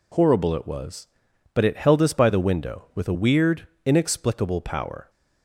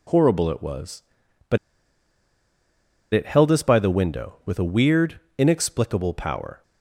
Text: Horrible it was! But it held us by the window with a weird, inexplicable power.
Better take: first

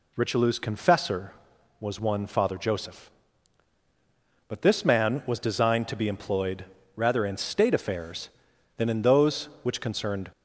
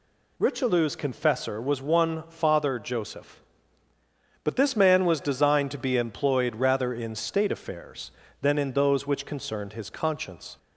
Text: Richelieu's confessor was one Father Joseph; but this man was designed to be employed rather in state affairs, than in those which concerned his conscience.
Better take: second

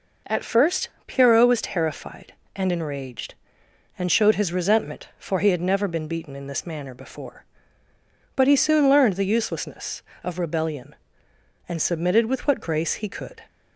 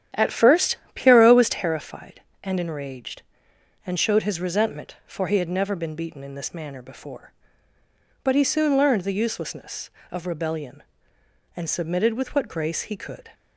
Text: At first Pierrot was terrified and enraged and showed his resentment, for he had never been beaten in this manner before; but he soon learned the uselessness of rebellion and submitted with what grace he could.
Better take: first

